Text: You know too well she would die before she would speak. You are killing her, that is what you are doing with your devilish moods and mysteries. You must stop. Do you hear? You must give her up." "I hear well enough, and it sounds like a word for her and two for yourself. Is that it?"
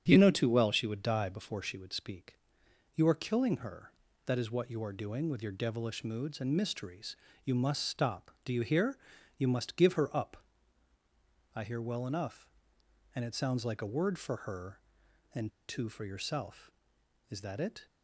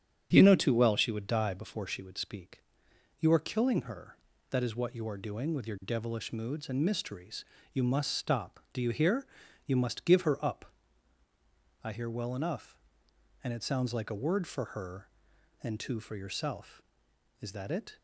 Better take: second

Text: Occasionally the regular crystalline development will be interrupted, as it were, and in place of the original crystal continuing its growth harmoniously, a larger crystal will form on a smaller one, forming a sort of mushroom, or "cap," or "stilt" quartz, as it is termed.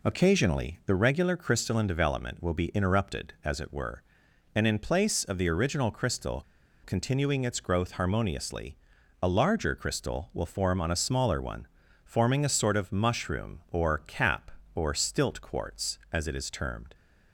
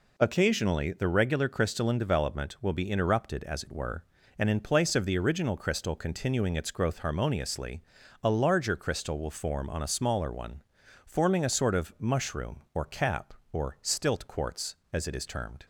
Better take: second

